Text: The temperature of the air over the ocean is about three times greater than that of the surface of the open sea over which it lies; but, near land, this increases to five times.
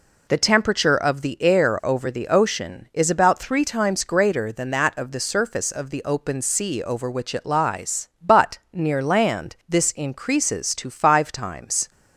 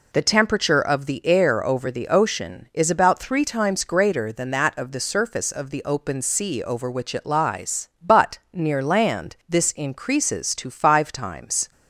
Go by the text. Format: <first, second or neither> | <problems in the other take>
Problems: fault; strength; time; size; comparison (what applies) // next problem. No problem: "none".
neither | none